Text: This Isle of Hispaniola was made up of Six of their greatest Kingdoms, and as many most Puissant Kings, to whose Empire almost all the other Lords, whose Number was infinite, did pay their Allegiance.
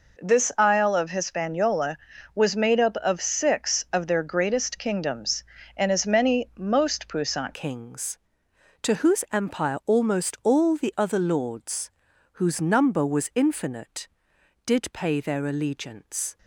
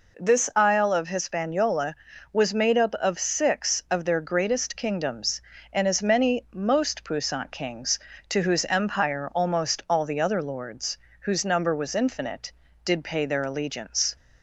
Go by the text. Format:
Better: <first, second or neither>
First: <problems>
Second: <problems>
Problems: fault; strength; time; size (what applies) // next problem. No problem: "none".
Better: second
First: changes voice at "Kings"; from 7.5 s on; 8.8 s long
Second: none